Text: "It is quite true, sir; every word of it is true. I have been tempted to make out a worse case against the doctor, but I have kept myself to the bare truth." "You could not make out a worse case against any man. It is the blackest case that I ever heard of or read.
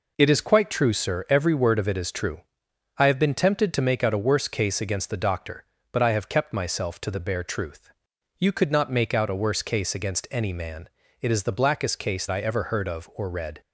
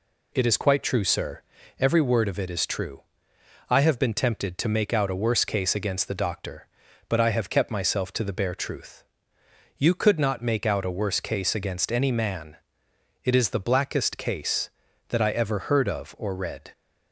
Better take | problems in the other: second | skips "that"; at 12.2 s

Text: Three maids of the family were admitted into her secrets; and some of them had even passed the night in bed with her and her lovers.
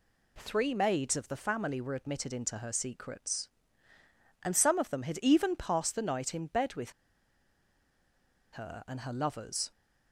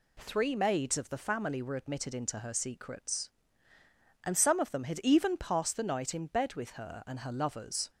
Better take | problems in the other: second | pauses between "with" and "her"; strong; at 6.9 s; 1.6 s long

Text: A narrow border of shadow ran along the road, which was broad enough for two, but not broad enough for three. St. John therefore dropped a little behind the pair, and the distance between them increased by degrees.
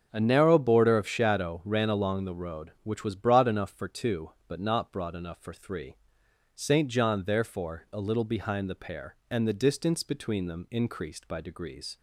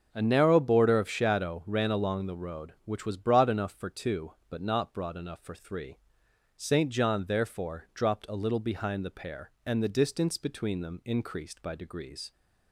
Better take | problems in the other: second | starts louder than the rest; until 1.1 s; 6.5 dB // skips "dropped"; at 7.8 s

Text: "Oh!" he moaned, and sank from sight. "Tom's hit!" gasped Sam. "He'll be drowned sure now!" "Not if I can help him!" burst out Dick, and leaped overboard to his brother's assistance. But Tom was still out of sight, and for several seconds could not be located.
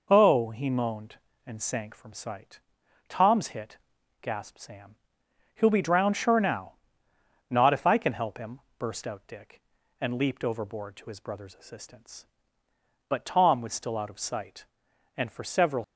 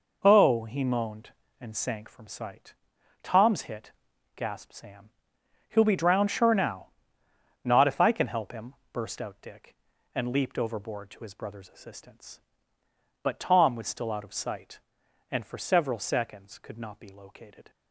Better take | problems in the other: second | stops before "seconds could not be located"; at 15.8 s

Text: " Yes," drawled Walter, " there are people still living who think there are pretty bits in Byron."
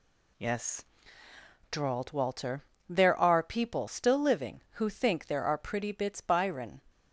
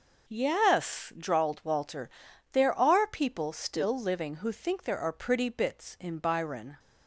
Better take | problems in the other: second | skips "in"; at 6.2 s

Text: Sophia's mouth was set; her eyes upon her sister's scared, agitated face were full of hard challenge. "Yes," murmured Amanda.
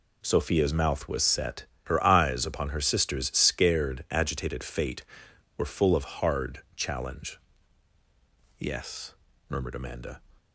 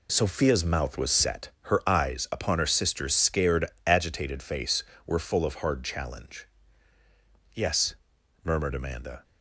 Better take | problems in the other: second | says "fate" for "face"; at 4.6 s // pauses between "of" and "hard"; slight; at 6.0 s; 0.18 s long

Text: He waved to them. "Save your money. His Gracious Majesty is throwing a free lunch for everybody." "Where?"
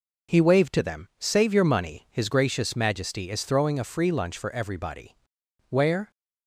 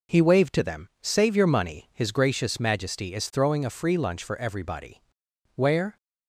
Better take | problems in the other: neither | none

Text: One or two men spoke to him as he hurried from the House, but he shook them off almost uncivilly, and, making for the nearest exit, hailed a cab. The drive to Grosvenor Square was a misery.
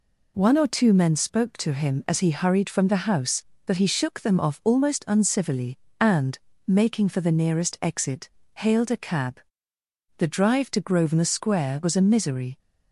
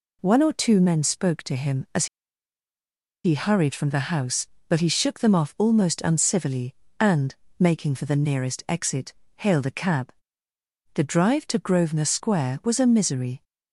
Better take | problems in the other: first | pauses between "as" and "he"; at 2.0 s; 1.1 s long

